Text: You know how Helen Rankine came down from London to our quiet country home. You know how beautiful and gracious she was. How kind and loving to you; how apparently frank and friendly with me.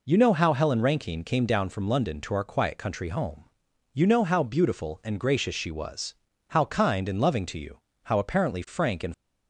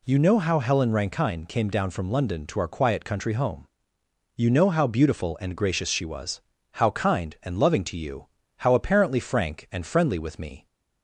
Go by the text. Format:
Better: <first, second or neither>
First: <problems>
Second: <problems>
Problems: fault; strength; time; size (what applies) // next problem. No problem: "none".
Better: second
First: stops before "friendly with me"; at 9.1 s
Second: none